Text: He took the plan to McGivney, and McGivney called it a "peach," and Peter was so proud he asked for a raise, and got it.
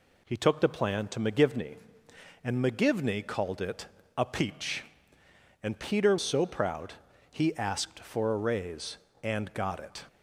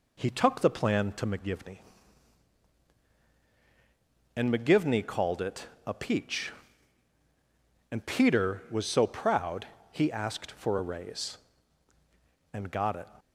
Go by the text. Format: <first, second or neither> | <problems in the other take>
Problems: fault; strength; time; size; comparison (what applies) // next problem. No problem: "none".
second | pauses between "it" and "a"; slight; at 3.8 s; 0.32 s long; slight in the second // skips "was"; at 6.1 s // pauses between "proud" and "he"; slight; at 6.9 s; 0.36 s long; slight in the second